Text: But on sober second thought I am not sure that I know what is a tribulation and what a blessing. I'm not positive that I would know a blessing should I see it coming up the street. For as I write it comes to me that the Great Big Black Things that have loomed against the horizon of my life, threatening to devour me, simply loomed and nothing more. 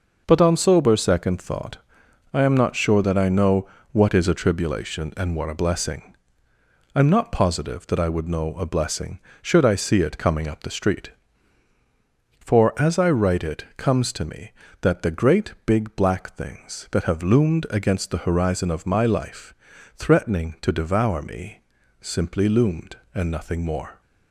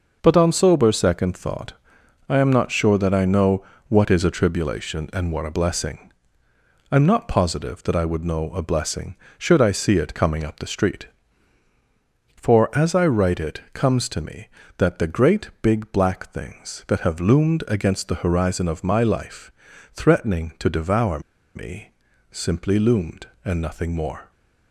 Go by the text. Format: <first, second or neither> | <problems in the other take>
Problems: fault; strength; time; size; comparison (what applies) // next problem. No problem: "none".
first | pauses between "thought" and "I"; noticeable; at 1.7 s; 0.54 s long; noticeable in the first // pauses between "know" and "what"; slight; at 3.6 s; 0.24 s long; slight in the first // pauses between "devour" and "me"; slight; at 21.1 s; 0.35 s long